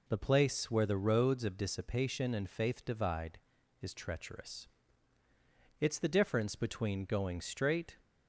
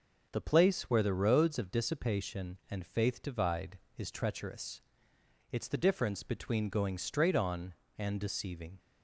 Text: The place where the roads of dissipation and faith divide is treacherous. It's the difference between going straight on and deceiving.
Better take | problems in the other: second | stops before "on and deceiving"; at 8.0 s

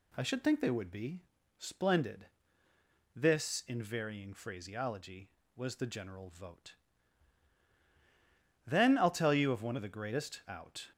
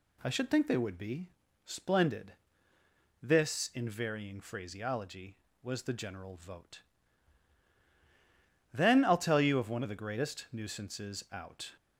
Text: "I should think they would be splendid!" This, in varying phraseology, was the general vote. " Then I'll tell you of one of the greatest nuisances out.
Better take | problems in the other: second | pauses between "be" and "splendid"; slight; at 1.2 s; 0.34 s long; slight in the second // skips "nuisances"; at 10.4 s

